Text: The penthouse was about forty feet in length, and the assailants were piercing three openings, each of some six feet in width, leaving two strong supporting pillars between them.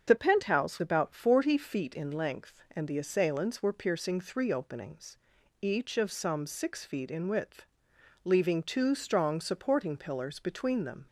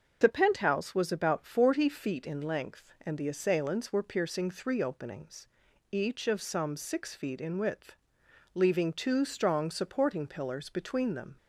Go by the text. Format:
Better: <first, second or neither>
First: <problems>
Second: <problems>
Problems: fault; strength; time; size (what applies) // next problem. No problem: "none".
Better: second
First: starts louder than the rest; until 1.0 s; 7 dB // skips "was"; at 0.8 s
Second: starts louder than the rest; until 1.2 s; 6.5 dB